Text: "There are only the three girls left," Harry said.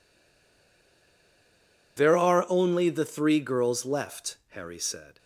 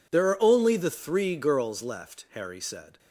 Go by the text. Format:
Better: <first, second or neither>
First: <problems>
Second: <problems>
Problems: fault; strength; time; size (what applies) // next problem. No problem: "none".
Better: second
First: stays silent before the first word; noticeable; until 1.9 s; 1.9 s long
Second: none